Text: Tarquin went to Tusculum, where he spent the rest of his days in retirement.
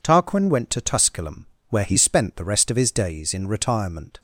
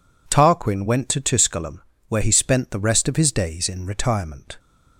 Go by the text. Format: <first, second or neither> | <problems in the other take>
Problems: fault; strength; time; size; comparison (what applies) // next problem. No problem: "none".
neither | none